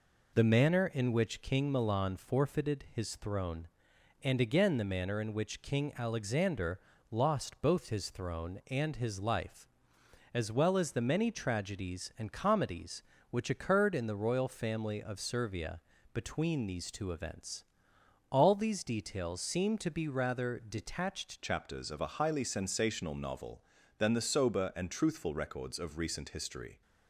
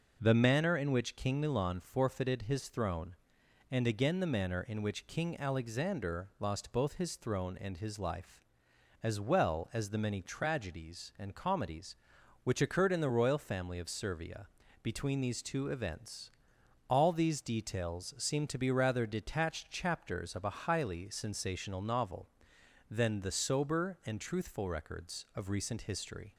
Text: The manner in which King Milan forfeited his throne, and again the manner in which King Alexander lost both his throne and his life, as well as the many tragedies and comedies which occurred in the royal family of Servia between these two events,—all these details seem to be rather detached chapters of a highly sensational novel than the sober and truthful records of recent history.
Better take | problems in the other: second | pauses between "Alexander" and "lost"; slight; at 6.7 s; 0.32 s long // pauses between "Servia" and "between"; slight; at 15.7 s; 0.34 s long; slight in the second // changes voice at "chapters"; from 21.4 s on; 5.4 s long

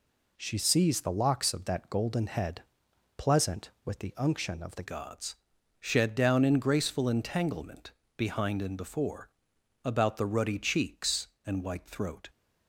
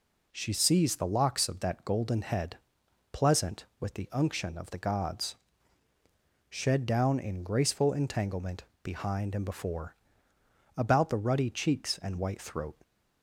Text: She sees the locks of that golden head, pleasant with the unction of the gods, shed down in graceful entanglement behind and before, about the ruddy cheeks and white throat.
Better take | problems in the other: second | changes voice at "gods"; from 4.8 s on; 7.4 s long // pauses between "entanglement" and "behind"; slight; at 7.9 s; 0.24 s long; slight in the second

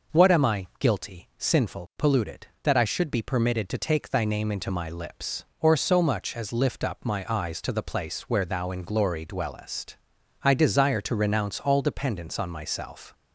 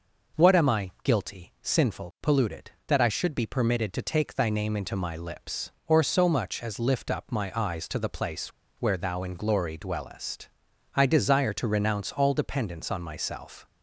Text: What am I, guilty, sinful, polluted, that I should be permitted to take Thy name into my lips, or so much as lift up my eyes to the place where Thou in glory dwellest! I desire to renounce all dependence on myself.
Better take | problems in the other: first | pauses between "place" and "where"; slight; at 8.4 s; 0.28 s long

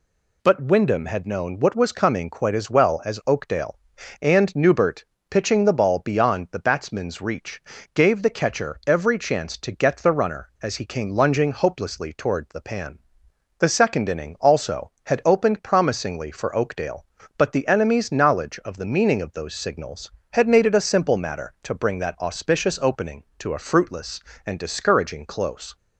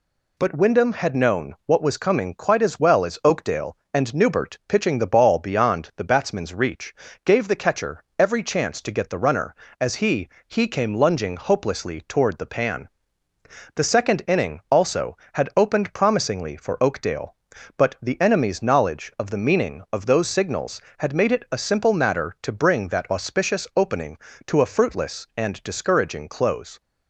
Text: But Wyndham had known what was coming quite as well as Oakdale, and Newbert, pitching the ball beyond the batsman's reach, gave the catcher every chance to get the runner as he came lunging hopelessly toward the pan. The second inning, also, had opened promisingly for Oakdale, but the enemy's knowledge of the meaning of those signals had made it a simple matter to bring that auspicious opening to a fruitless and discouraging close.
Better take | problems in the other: first | pauses between "catcher" and "every"; slight; at 8.0 s; 0.16 s long // says "he" twice; at 10.4 s

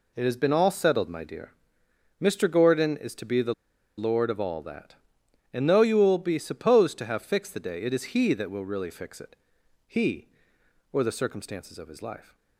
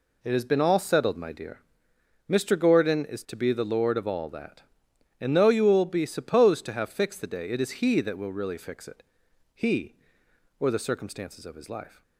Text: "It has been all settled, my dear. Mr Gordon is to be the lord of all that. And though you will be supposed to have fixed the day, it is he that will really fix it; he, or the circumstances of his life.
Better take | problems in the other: second | pauses between "the" and "lord"; at 3.5 s; 0.44 s long

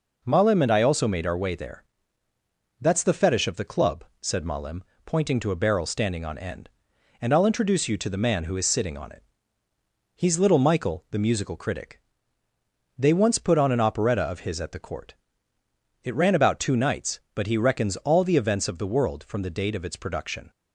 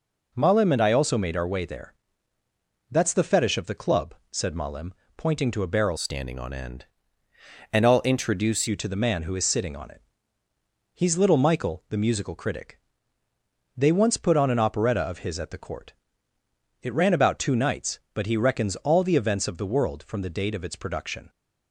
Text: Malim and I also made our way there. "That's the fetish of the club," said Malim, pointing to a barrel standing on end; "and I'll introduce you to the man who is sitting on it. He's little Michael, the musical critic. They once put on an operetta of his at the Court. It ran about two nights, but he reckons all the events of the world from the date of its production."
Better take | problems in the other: first | changes voice from "standing" to "introduce"; from 5.9 to 8.6 s; 2.7 s long

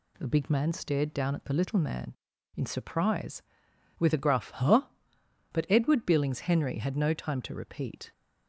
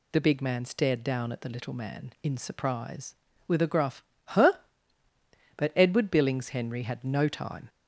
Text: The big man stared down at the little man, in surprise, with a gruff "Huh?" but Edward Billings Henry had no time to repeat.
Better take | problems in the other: first | pauses between "gruff" and "Huh"; slight; at 4.0 s; 0.22 s long // stops before "to repeat"; at 7.6 s

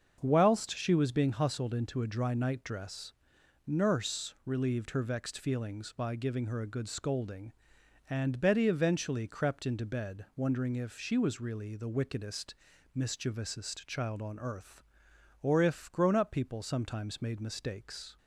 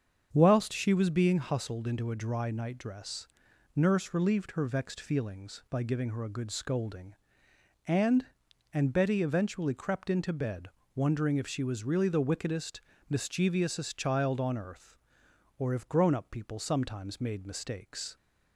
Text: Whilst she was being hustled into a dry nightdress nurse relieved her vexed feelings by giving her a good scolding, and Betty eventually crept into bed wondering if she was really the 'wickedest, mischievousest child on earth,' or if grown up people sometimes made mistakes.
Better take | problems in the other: first | starts louder than the rest; strong; until 1.3 s; 7 dB; also in the first // pauses between "nightdress" and "nurse"; noticeable; at 3.2 s; 0.48 s long; noticeable in the first // says "and" twice; at 8.7 s // pauses between "bed" and "wondering"; slight; at 10.6 s; 0.26 s long

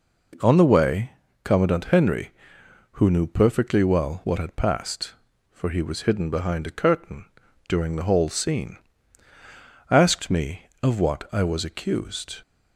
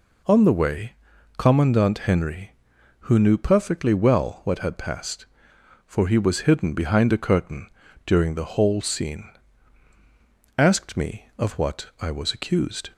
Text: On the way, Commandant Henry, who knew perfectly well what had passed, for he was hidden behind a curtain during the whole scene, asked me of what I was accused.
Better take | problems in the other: neither | pauses between "curtain" and "during"; the same in both

